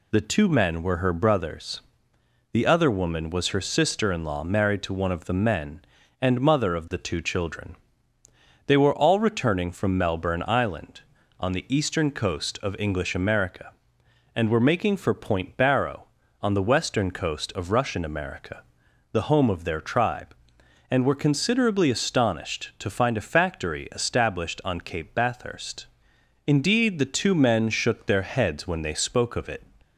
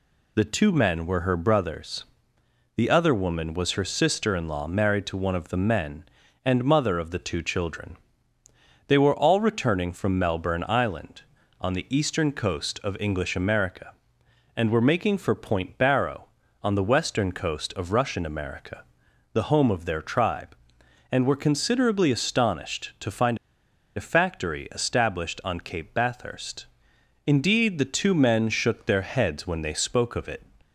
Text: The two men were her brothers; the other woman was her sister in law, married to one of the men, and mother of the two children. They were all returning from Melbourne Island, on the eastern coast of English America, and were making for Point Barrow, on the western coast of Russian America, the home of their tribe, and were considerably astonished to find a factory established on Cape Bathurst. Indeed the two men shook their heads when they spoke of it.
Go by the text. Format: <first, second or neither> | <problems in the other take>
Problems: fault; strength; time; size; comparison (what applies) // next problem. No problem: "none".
first | pauses between "find" and "a"; noticeable; at 23.3 s; 0.59 s long